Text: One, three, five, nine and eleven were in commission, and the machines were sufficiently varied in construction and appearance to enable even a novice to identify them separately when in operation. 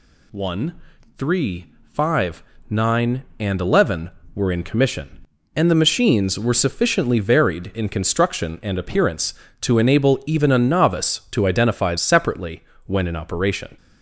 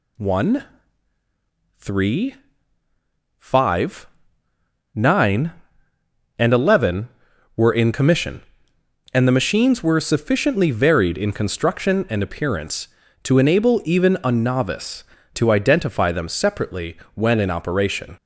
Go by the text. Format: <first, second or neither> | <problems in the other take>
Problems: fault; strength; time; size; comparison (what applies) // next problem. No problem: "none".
second | skips "them"; at 11.9 s // pauses between "separately" and "when"; slight; at 12.6 s; 0.22 s long; slight in the second